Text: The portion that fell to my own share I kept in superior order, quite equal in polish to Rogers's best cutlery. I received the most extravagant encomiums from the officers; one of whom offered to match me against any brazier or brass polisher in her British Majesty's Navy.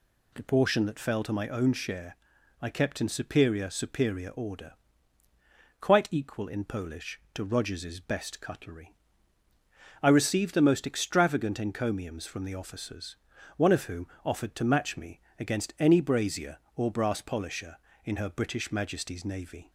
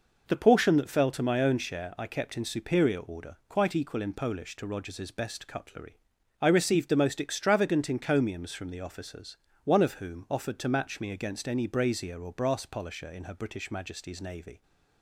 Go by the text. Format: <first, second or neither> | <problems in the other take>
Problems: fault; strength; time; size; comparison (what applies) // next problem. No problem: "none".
second | pauses between "share" and "I"; at 2.1 s; 0.44 s long // says "superior" twice; at 3.6 s // pauses between "whom" and "offered"; slight; at 14.0 s; 0.18 s long // pauses between "me" and "against"; slight; at 15.2 s; 0.18 s long